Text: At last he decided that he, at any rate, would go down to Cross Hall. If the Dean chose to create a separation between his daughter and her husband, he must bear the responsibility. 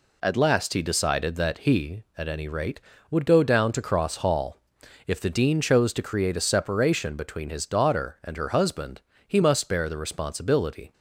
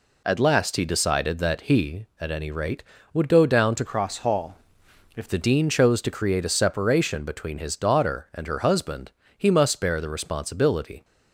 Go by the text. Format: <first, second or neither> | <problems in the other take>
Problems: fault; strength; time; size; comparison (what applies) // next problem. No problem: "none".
first | changes voice from "Cross" to "If"; from 3.8 to 5.2 s; 1.4 s long